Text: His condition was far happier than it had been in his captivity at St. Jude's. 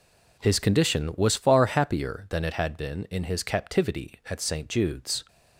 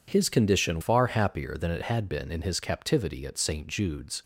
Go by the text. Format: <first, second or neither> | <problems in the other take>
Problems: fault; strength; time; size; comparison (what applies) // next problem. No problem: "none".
first | skips "was"; at 0.8 s